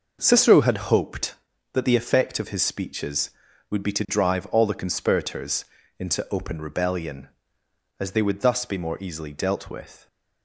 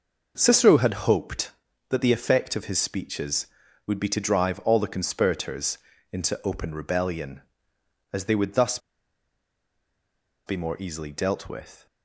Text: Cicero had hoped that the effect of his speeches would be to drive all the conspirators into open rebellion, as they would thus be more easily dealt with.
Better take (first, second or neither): first